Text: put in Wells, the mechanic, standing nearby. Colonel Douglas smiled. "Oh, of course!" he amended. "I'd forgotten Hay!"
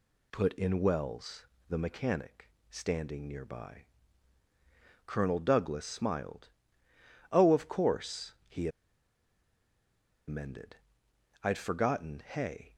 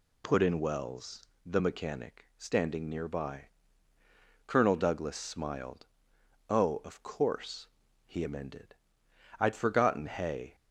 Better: second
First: pauses between "he" and "amended"; strong; at 8.6 s; 1.5 s long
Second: none

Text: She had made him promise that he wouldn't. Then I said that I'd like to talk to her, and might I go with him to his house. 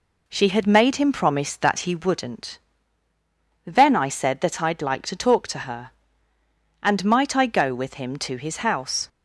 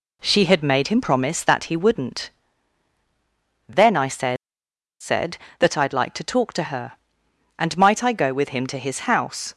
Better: first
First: none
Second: says "said" twice; at 4.9 s

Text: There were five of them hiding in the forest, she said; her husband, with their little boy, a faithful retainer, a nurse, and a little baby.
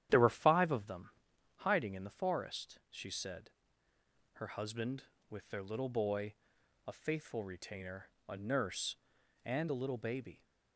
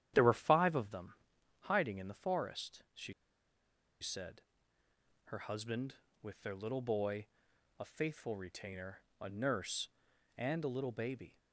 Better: first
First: starts louder than the rest; strong; until 1.6 s; 10.5 dB // pauses between "them" and "hiding"; noticeable; at 1.0 s; 0.50 s long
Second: starts louder than the rest; strong; until 1.6 s; 10.5 dB // pauses between "them" and "hiding"; noticeable; at 1.1 s; 0.50 s long // pauses between "she" and "said"; noticeable; at 3.1 s; 0.88 s long

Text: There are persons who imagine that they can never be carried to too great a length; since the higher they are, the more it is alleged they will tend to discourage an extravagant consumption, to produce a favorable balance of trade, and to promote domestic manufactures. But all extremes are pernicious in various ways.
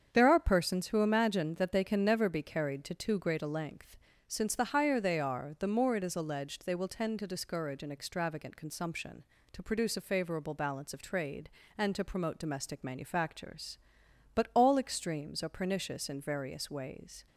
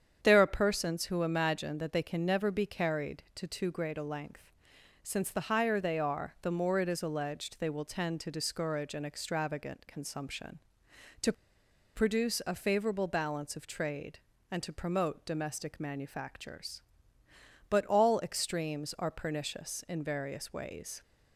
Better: first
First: starts louder than the rest; strong; until 1.1 s; 7.5 dB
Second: starts louder than the rest; strong; until 1.2 s; 8 dB // pauses between "to" and "produce"; noticeable; at 11.3 s; 0.62 s long

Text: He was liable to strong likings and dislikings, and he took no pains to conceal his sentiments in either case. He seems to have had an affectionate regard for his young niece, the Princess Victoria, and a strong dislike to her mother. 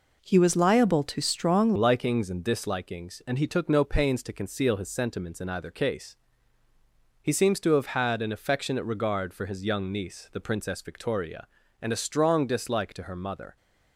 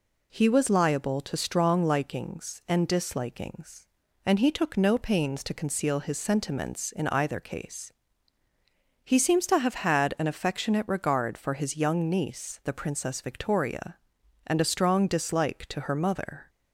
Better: second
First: changes voice at "likings"; from 1.7 s on; 11.8 s long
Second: none

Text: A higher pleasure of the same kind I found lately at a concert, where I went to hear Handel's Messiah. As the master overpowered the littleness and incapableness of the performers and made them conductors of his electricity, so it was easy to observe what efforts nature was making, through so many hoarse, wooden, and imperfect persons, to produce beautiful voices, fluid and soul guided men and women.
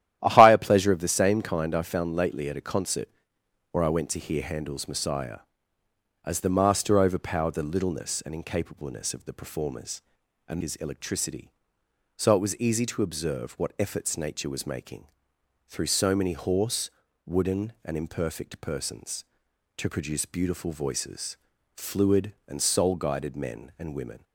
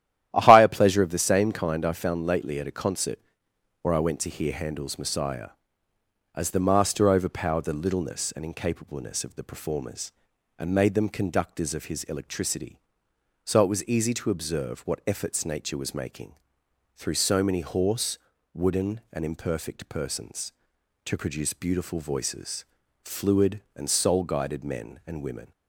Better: second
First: starts louder than the rest; strong; until 1.2 s; 12 dB // skips "made them conductors of"; at 10.6 s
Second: starts louder than the rest; strong; until 1.3 s; 12 dB

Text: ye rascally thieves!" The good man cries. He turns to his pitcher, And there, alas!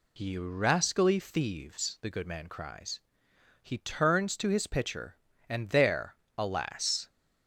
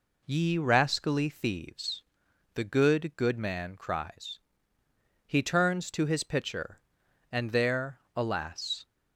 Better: first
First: none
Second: says "good" twice; at 3.1 s

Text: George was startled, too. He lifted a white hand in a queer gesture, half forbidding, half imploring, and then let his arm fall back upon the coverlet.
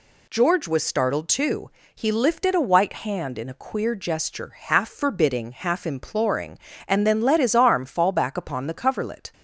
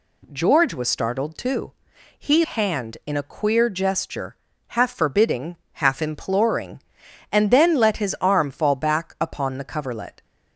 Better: first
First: none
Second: skips "lifted a white"; at 2.4 s

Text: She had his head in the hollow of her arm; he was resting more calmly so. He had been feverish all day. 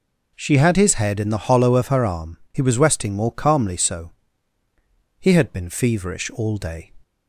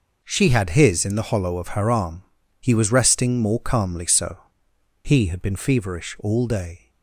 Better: first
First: none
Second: skips "head"; at 1.0 s

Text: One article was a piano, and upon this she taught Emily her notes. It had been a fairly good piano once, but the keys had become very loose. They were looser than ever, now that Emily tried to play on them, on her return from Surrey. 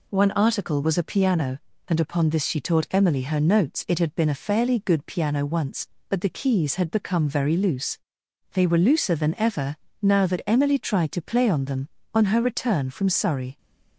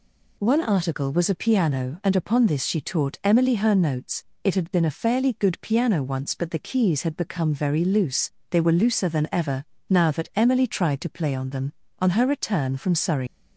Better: first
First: none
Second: leaves "Surrey" unfinished; at 13.2 s; 130 ms

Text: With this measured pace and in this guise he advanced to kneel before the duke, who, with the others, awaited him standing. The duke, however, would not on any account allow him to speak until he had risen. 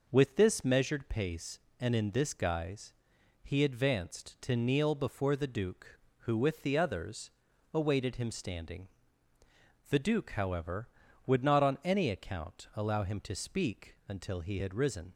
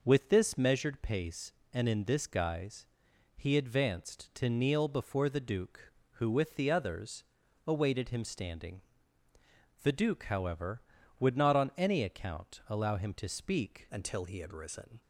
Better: first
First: pauses between "guise" and "he"; noticeable; at 2.9 s; 0.50 s long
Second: pauses between "guise" and "he"; noticeable; at 2.8 s; 0.50 s long // changes voice at "until"; from 13.9 s on; 1.1 s long

